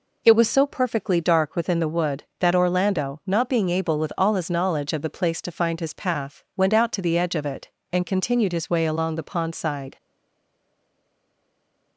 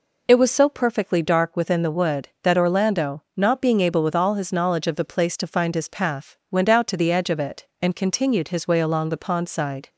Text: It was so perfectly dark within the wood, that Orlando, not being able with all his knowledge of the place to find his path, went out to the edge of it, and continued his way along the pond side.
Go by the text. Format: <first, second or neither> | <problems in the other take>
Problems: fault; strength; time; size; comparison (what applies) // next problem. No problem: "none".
second | stays silent after the last word; noticeable; from 9.9 s on; 2.0 s long